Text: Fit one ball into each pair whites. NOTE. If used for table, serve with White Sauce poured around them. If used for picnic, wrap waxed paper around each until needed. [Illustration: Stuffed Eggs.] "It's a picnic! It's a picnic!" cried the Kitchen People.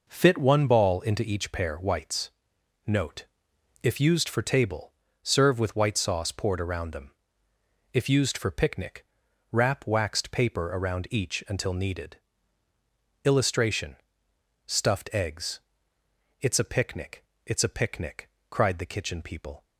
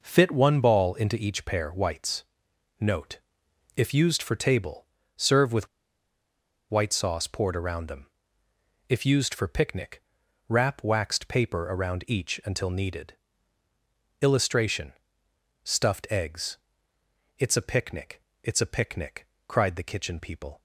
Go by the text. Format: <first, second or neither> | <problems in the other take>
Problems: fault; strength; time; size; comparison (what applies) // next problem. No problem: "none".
first | pauses between "with" and "White"; at 5.6 s; 1.0 s long